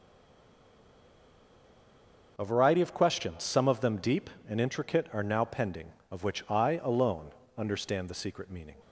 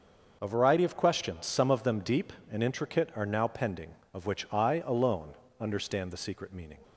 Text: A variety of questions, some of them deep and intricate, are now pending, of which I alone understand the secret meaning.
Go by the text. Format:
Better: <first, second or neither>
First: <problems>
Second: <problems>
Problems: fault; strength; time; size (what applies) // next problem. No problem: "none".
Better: second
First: stays silent before the first word; until 2.3 s; 2.3 s long // starts louder than the rest; noticeable; until 3.3 s; 6 dB // pauses between "alone" and "understand"; slight; at 7.2 s; 0.26 s long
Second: starts louder than the rest; noticeable; until 1.4 s; 6 dB // pauses between "alone" and "understand"; slight; at 5.3 s; 0.26 s long